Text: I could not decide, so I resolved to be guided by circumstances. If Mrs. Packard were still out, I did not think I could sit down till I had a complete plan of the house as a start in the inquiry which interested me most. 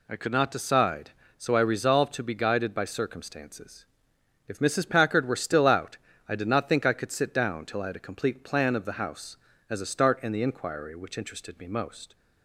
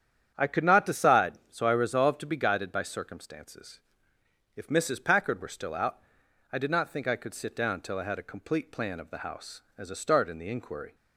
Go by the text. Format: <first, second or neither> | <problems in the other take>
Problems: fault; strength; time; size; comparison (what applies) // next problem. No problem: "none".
first | starts louder than the rest; strong; until 1.3 s; 9 dB // stops before "which interested me most"; at 10.9 s